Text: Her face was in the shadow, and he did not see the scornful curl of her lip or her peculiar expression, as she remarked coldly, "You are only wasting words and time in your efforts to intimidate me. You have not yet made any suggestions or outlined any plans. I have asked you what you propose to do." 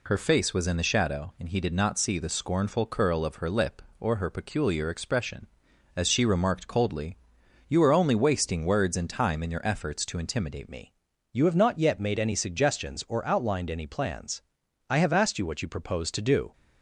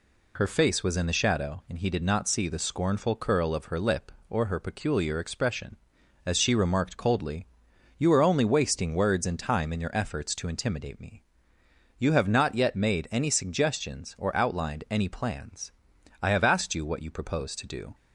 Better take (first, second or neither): second